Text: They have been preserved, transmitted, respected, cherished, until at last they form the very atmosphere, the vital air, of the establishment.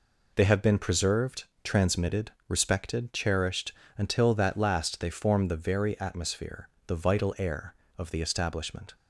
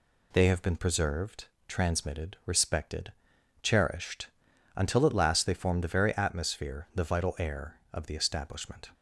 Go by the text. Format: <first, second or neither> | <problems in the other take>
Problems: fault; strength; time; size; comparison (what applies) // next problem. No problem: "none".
second | says "that" for "at"; at 4.3 s